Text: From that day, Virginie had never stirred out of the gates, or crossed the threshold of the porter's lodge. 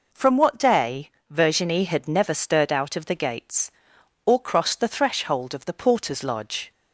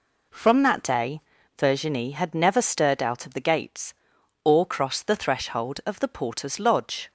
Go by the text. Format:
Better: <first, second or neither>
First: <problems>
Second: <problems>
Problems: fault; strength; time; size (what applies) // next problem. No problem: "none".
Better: second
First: says "what" for "that"; at 0.3 s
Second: none